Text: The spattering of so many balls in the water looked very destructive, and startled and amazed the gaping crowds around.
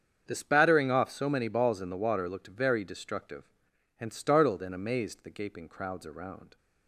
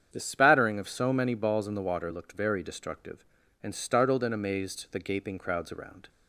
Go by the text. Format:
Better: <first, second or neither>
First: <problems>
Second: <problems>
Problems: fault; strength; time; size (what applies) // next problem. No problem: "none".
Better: second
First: starts louder than the rest; strong; until 1.2 s; 7.5 dB // says "off" for "of"; at 0.9 s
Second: starts louder than the rest; strong; until 1.1 s; 8 dB